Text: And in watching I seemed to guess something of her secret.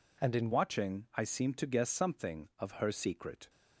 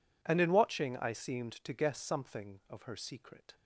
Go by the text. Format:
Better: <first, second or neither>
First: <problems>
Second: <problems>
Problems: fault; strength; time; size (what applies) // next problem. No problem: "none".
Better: second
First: changes voice at "watching"; from 0.5 s on; 2.9 s long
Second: none